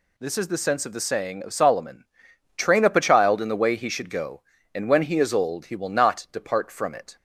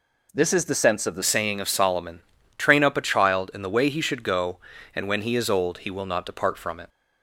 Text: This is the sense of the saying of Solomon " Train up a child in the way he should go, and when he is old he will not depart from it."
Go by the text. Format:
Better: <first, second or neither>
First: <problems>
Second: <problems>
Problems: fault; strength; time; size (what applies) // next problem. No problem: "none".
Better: first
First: none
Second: changes voice at "saying"; from 1.2 s on; 5.6 s long